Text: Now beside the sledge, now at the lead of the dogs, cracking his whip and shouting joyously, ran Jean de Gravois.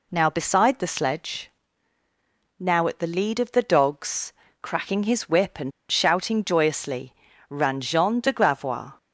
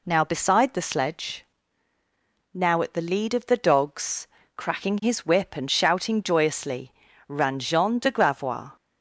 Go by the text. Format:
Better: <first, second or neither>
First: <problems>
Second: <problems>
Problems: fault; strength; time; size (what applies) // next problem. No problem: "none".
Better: second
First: pauses between "and" and "shouting"; slight; at 5.7 s; 0.19 s long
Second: none